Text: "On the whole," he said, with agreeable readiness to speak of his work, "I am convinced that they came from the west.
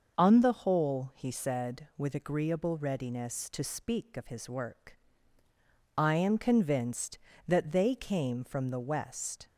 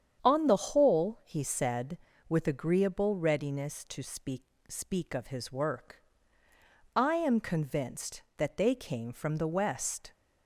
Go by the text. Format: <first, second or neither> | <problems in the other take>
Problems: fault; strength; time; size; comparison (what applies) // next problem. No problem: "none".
first | starts louder than the rest; strong; until 1.2 s; 8 dB; noticeable in the first // says "speak" twice; at 4.6 s